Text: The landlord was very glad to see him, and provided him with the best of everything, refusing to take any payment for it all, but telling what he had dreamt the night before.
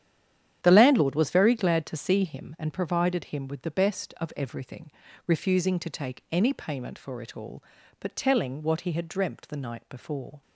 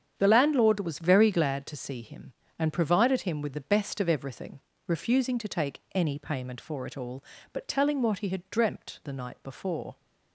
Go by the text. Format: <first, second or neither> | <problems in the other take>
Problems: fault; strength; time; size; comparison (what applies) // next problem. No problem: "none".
second | stays silent before the first word; slight; until 0.6 s; 0.6 s long // starts louder than the rest; strong; until 1.6 s; 10 dB; strong in the second